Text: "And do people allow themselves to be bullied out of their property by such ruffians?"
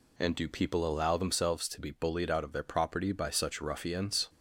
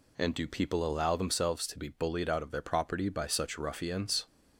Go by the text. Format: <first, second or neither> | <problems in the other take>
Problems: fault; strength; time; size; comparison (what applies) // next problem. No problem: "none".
neither | none